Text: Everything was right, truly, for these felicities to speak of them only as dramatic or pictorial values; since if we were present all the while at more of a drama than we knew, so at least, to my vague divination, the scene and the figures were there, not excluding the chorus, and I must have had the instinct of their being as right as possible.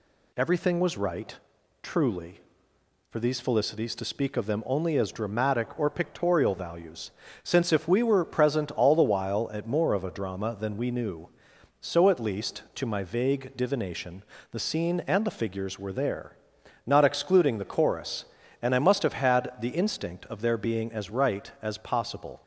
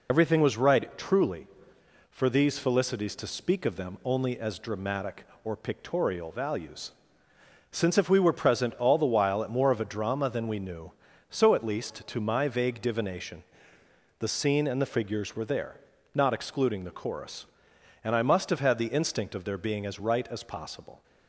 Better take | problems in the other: first | loses the start of "Everything"; at 0.0 s; 70 ms

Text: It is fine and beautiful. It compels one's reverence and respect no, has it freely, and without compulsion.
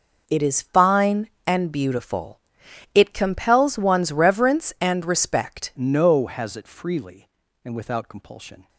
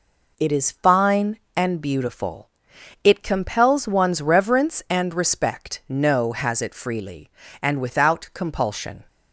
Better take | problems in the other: second | changes voice at "no"; from 5.7 s on; 2.9 s long

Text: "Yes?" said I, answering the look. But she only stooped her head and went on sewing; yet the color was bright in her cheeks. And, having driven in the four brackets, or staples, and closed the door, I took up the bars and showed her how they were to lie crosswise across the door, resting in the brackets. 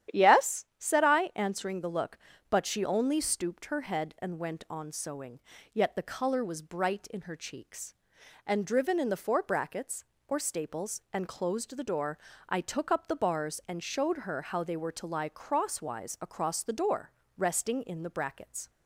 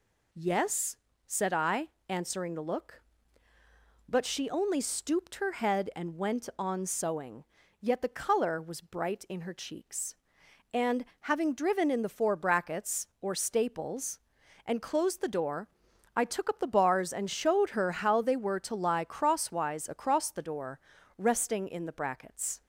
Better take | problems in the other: second | starts louder than the rest; strong; until 1.2 s; 10.5 dB // skips "having"; at 8.6 s

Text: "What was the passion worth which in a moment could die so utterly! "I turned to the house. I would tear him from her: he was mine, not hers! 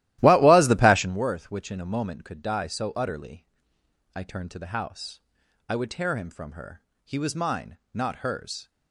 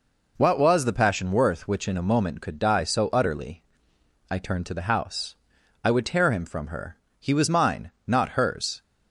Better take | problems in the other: second | starts louder than the rest; strong; until 1.2 s; 15 dB

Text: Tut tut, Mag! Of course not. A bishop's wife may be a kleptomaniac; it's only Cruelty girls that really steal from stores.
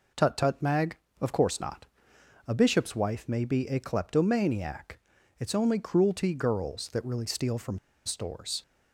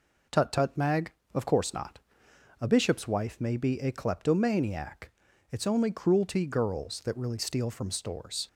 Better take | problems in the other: second | pauses between "from" and "stores"; slight; at 7.7 s; 0.27 s long

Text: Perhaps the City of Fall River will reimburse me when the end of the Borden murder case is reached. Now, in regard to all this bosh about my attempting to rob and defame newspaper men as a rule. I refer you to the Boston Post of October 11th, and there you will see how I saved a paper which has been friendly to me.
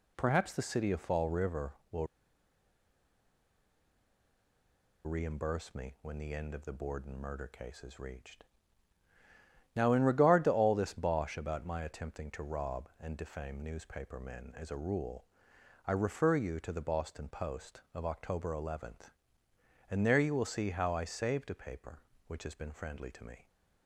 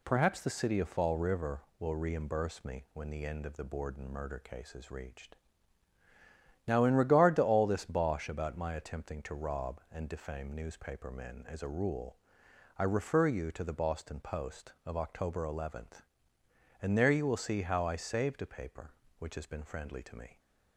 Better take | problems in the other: second | pauses between "will" and "reimburse"; strong; at 2.0 s; 2.9 s long

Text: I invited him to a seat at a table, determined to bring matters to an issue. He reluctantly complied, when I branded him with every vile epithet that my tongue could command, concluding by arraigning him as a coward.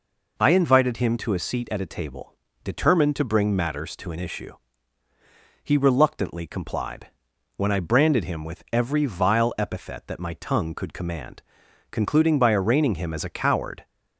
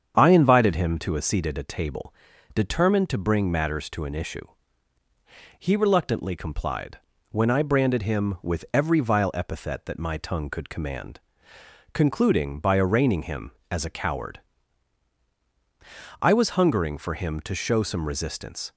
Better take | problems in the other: first | starts louder than the rest; strong; until 1.2 s; 7.5 dB // goes on to say "I was hungering for him to show some resistance"; strong; from 16.2 s on; 2.5 s long

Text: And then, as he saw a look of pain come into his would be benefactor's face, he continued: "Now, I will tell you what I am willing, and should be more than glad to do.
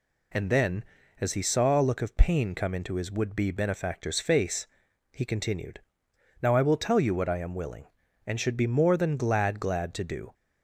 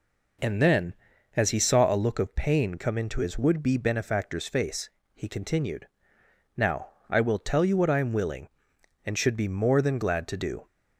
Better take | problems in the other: second | says "glad" twice; at 9.5 s

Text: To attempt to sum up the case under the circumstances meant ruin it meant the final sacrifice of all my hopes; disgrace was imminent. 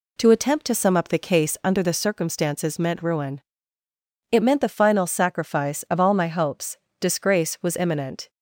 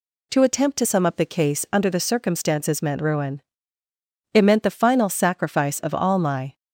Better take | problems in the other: first | pauses between "ruin" and "it"; noticeable; at 3.4 s; 0.92 s long; noticeable in the first // stops before "hopes disgrace was imminent"; at 6.5 s

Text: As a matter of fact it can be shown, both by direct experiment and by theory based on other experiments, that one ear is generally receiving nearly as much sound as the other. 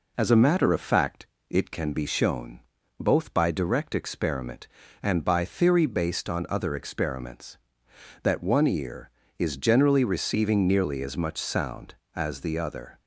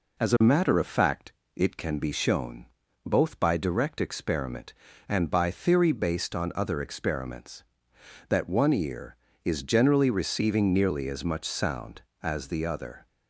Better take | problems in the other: neither | pauses between "fact" and "it"; slight; the same in both

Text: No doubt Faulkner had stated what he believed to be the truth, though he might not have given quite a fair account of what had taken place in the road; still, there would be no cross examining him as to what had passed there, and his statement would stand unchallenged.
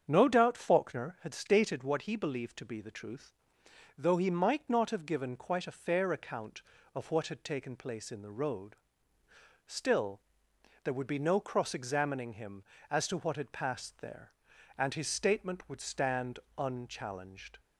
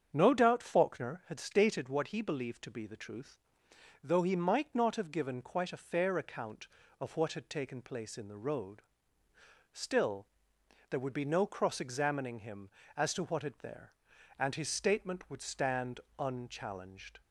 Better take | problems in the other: first | starts louder than the rest; strong; until 1.1 s; 7.5 dB; strong in the first // skips "passed"; at 13.5 s // pauses between "stand" and "unchallenged"; slight; at 15.9 s; 0.20 s long; slight in the first

